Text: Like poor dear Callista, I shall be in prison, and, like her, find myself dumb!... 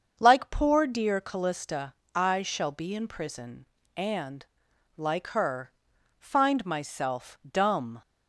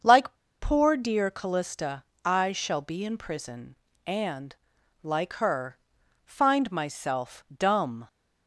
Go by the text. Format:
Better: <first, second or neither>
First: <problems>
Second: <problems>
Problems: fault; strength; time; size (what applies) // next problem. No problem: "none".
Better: first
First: starts louder than the rest; until 1.2 s; 7 dB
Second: starts louder than the rest; until 1.3 s; 7 dB // pauses between "Like" and "poor"; slight; at 0.3 s; 0.29 s long